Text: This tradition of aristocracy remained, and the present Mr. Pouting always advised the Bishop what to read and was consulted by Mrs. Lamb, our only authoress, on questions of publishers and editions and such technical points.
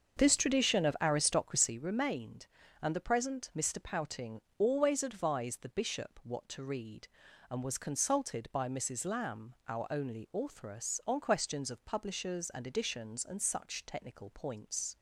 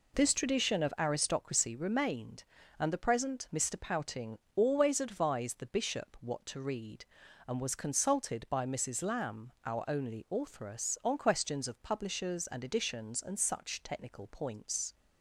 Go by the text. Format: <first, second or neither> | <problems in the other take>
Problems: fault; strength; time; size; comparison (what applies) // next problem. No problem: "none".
second | starts louder than the rest; until 1.9 s; 6.5 dB // pauses between "Pouting" and "always"; slight; at 4.4 s; 0.16 s long; slight in the second